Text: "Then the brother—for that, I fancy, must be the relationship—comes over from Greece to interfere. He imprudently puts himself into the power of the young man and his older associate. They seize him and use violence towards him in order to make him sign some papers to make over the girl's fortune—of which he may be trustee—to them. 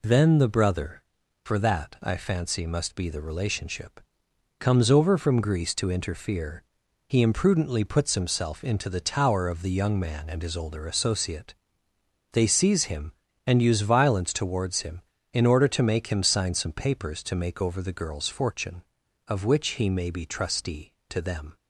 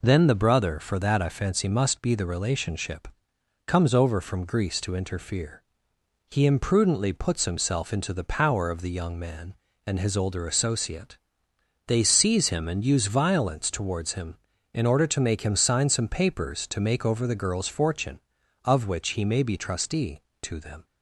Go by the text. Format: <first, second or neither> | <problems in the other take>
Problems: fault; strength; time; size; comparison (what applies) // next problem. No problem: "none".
second | says "tower" for "power"; at 8.9 s